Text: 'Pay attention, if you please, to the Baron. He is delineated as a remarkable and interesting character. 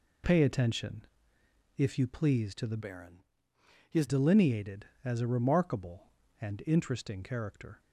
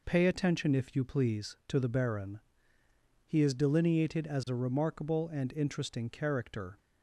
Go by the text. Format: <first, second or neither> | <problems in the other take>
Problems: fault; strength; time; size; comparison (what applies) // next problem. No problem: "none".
second | changes voice from "Baron" to "is"; from 2.8 to 4.0 s; 1.2 s long